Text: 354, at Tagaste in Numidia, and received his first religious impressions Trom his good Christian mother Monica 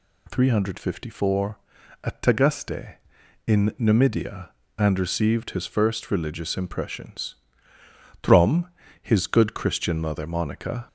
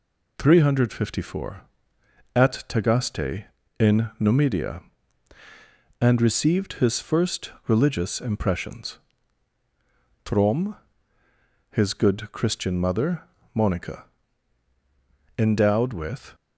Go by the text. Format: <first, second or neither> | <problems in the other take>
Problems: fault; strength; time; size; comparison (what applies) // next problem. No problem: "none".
first | pauses between "first" and "religious"; slight; at 7.5 s; 0.16 s long // pauses between "impressions" and "Trom"; strong; at 8.9 s; 1.2 s long; noticeable in the first // pauses between "Trom" and "his"; noticeable; at 10.7 s; 0.94 s long; slight in the first // pauses between "mother" and "Monica"; slight; at 13.2 s; 0.32 s long // goes on to say "Endowed with"; noticeable; from 15.3 s on; 0.96 s long